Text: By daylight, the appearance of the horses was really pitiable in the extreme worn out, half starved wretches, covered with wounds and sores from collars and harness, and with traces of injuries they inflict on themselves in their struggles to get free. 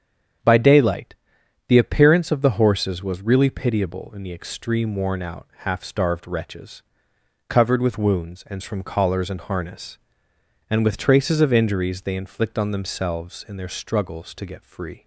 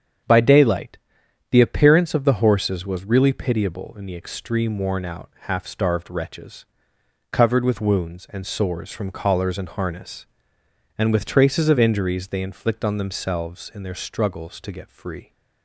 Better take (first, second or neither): second